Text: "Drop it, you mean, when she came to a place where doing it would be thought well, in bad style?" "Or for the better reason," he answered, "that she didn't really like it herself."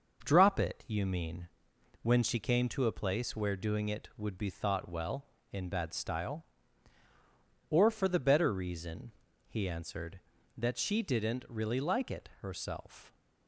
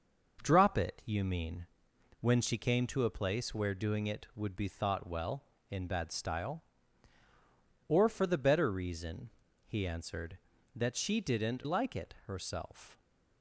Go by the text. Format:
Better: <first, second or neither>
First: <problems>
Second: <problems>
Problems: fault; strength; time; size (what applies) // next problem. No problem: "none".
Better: first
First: none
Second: skips "really"; at 11.6 s